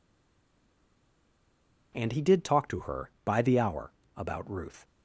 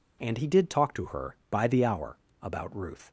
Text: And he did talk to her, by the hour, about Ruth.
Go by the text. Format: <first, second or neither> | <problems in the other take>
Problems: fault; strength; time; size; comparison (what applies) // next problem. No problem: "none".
second | stays silent before the first word; noticeable; until 1.9 s; 1.9 s long